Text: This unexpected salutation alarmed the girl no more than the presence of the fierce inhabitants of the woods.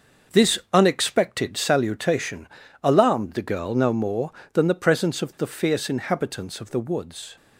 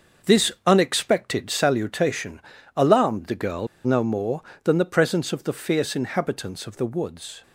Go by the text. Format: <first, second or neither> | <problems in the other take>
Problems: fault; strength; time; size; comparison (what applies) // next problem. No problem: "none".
first | starts louder than the rest; noticeable; until 1.3 s; 6 dB; noticeable in the first // pauses between "salutation" and "alarmed"; slight; at 2.4 s; 0.36 s long; slight in the first // pauses between "girl" and "no"; slight; at 3.6 s; 0.18 s long